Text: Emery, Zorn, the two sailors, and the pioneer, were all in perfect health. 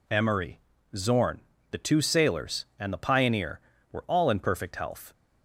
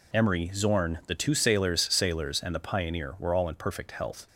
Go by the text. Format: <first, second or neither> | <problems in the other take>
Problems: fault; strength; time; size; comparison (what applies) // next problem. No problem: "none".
first | says "sailors" twice; at 1.9 s